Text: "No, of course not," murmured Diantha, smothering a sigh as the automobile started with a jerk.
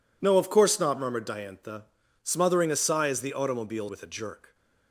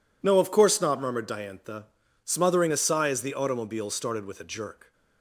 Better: second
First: skips "started"; at 3.8 s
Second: none

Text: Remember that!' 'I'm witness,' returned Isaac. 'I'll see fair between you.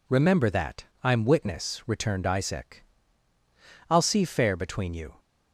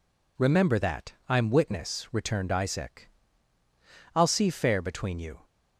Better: neither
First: none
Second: none

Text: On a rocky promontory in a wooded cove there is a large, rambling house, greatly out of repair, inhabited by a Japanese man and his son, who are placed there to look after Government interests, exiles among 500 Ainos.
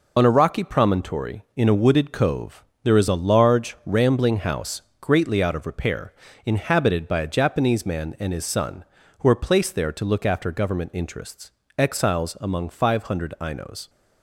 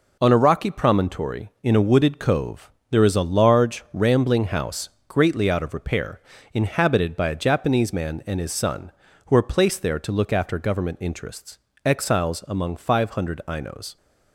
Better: second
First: loses the start of "On"; at 0.1 s; 40 ms // pauses between "cove" and "there"; slight; at 2.6 s; 0.18 s long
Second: pauses between "cove" and "there"; slight; at 2.7 s; 0.18 s long

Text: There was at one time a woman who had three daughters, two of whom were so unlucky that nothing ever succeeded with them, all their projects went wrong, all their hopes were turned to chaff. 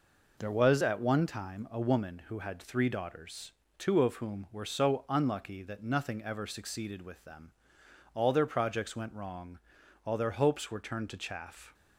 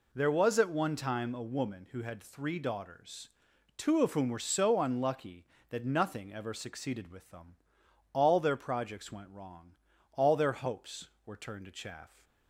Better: neither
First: none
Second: none

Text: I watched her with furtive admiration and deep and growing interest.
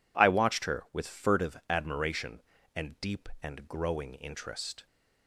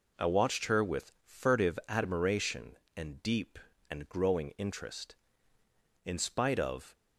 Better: first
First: none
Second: goes on to say "In spite of"; noticeable; from 6.0 s on; 0.88 s long

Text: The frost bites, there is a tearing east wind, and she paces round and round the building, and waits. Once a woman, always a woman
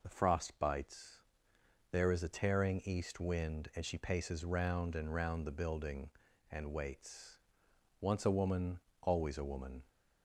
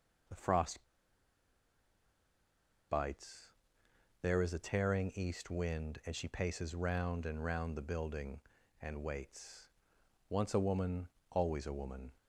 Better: first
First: none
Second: pauses between "frost" and "bites"; strong; at 0.8 s; 2.0 s long

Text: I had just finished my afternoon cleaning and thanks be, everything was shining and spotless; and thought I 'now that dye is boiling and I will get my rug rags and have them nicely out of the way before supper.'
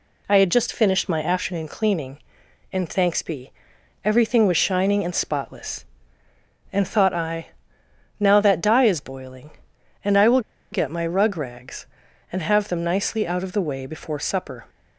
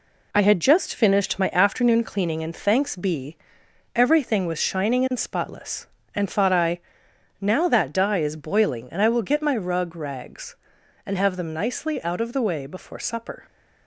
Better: second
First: pauses between "I" and "now"; noticeable; at 7.4 s; 0.72 s long // pauses between "will" and "get"; slight; at 10.3 s; 0.32 s long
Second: pauses between "I" and "now"; noticeable; at 6.7 s; 0.60 s long

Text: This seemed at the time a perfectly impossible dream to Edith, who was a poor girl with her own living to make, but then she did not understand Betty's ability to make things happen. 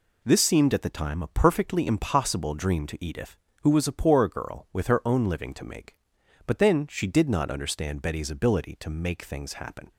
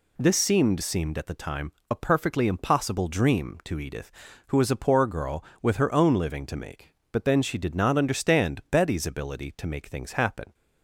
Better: first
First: none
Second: says "seemed" twice; at 0.8 s // pauses between "time" and "a"; slight; at 1.7 s; 0.18 s long

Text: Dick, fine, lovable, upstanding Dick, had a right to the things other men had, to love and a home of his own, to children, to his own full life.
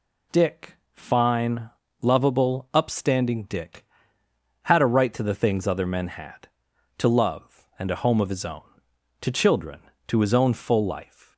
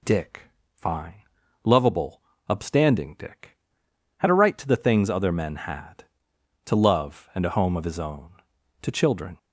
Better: first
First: none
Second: stops before "to his own full life"; at 9.3 s

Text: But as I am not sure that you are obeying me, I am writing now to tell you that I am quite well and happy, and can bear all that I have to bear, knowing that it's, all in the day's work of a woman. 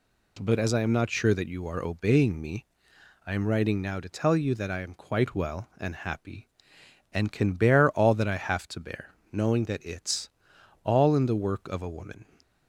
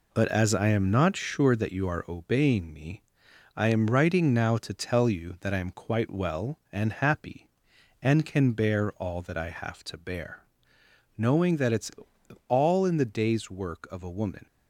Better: second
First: skips "day's"; at 11.3 s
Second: none

